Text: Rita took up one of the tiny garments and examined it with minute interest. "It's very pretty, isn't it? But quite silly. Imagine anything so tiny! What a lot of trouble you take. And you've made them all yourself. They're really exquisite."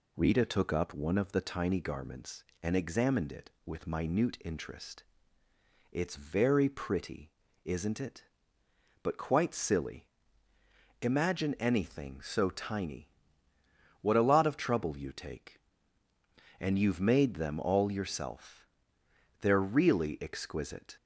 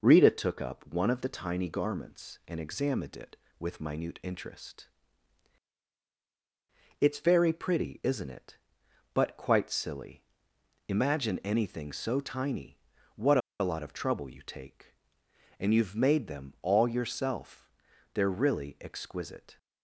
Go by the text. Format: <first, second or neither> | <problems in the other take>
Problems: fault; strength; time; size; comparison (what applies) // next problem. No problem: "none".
first | pauses between "What" and "a"; slight; at 13.3 s; 0.21 s long